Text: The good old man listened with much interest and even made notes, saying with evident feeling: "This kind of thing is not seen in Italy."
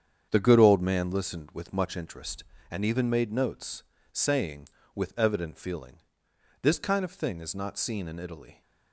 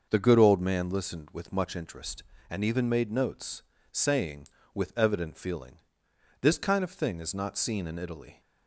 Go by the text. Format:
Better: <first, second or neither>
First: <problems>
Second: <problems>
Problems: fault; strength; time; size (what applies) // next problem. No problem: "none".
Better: second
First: gets quieter; strong; throughout; 9 dB // starts louder than the rest; strong; until 1.3 s; 8 dB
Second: starts louder than the rest; noticeable; until 1.1 s; 6 dB